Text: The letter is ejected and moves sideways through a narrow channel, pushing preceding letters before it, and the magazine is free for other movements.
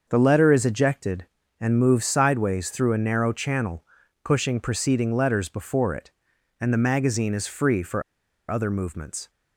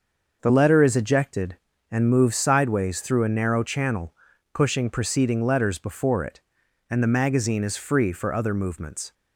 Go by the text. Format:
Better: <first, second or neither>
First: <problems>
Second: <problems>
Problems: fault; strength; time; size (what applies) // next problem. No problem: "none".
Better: second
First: starts louder than the rest; until 1.1 s; 6.5 dB // pauses between "for" and "other"; noticeable; at 8.0 s; 0.49 s long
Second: starts louder than the rest; until 1.4 s; 6 dB